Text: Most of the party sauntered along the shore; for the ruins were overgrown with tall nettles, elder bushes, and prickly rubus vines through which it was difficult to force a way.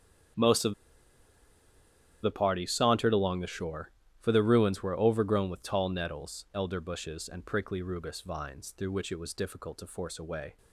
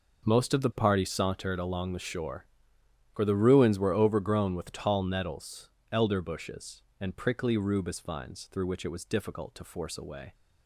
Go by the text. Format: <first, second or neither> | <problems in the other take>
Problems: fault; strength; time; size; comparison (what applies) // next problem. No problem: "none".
second | starts louder than the rest; strong; until 2.8 s; 8.5 dB // pauses between "of" and "the"; strong; at 0.7 s; 1.5 s long